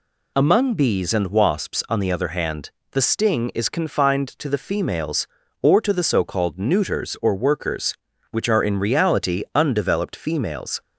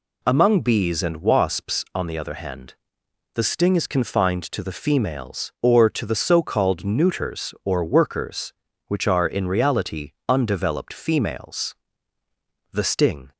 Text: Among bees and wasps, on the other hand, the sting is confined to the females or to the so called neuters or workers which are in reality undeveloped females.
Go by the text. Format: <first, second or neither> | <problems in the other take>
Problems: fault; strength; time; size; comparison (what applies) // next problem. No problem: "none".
first | pauses between "reality" and "undeveloped"; slight; at 10.1 s; 0.16 s long // goes on to say "The sting"; from 12.7 s on; 0.60 s long